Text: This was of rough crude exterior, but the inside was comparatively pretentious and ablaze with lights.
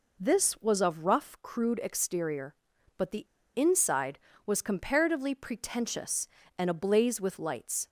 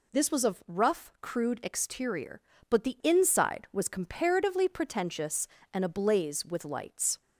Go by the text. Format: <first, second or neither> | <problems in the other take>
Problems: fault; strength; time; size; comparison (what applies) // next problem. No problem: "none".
second | pauses between "the" and "inside"; slight; at 3.2 s; 0.31 s long